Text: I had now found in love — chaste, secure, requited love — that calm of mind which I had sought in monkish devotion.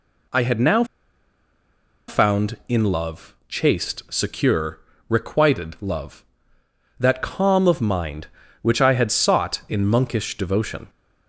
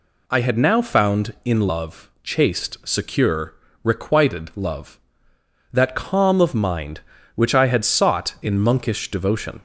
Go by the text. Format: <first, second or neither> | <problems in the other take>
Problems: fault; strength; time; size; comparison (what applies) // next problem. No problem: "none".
second | pauses between "now" and "found"; at 0.8 s; 1.2 s long